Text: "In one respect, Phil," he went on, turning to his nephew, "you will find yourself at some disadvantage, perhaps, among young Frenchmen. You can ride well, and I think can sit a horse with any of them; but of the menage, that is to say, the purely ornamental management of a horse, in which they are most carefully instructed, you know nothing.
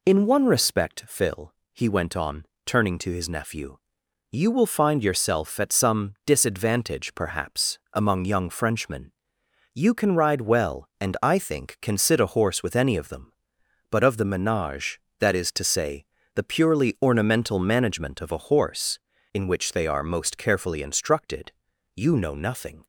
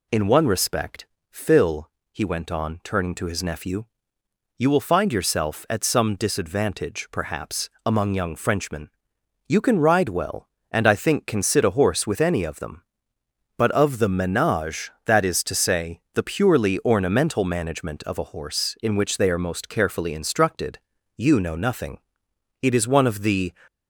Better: first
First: none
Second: goes on to say "It is one of the"; noticeable; from 22.6 s on; 0.90 s long

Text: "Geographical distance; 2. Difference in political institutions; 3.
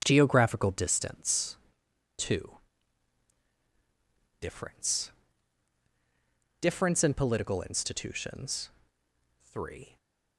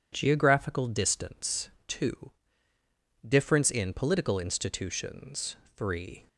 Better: second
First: starts louder than the rest; strong; until 1.0 s; 8 dB // says "Difference" twice; at 6.5 s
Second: none

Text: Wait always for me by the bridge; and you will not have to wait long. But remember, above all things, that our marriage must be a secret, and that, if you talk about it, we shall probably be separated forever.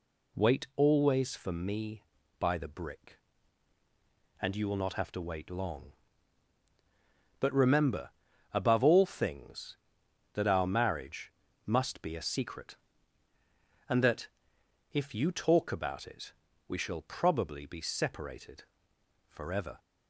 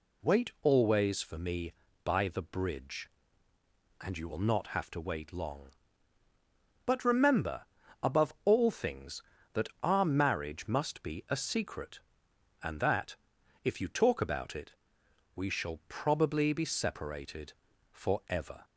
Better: second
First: says "brick" for "bridge"; at 2.6 s // pauses between "marriage" and "must"; slight; at 11.3 s; 0.34 s long // pauses between "separated" and "forever"; noticeable; at 18.6 s; 0.64 s long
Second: pauses between "separated" and "forever"; at 17.5 s; 0.40 s long

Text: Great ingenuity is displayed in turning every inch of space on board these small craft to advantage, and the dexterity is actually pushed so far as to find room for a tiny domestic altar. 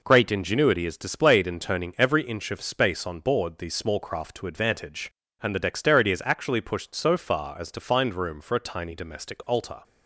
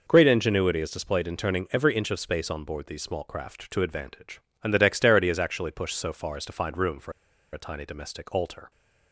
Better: first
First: none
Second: pauses between "for" and "a"; at 7.1 s; 0.41 s long

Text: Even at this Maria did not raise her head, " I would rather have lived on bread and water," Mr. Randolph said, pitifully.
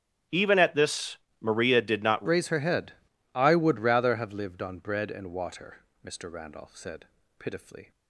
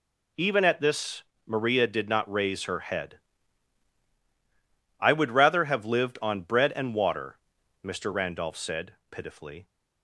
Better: second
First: starts louder than the rest; strong; until 1.5 s; 7.5 dB // pauses between "this" and "Maria"; slight; at 1.1 s; 0.24 s long // changes voice at "raise"; from 2.2 s on; 5.7 s long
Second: pauses between "this" and "Maria"; slight; at 1.2 s; 0.24 s long

